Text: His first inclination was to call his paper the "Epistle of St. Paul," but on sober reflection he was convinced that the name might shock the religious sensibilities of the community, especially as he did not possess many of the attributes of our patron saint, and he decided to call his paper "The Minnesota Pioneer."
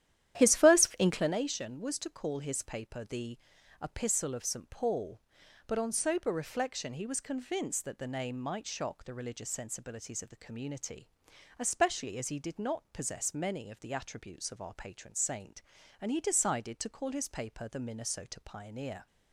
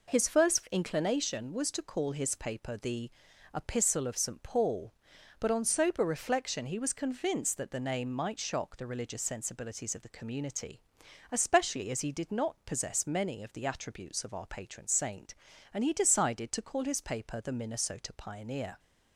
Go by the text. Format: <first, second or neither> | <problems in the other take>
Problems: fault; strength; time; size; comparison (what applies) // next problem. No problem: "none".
second | starts louder than the rest; strong; until 1.3 s; 11.5 dB // pauses between "the" and "Epistle"; at 3.3 s; 0.44 s long; also in the second